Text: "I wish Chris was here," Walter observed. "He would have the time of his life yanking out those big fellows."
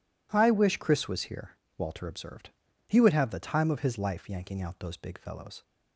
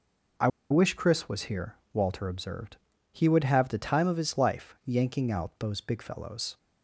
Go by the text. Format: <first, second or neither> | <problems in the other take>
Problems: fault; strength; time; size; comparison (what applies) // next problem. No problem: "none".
first | pauses between "I" and "wish"; slight; at 0.4 s; 0.21 s long